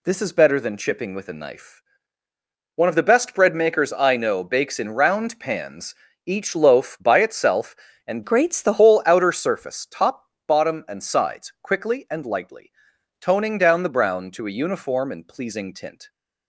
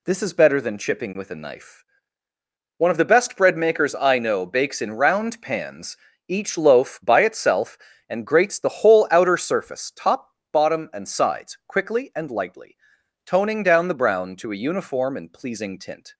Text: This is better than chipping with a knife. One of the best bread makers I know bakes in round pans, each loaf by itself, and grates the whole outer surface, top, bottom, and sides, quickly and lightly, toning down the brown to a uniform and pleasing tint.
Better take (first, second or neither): second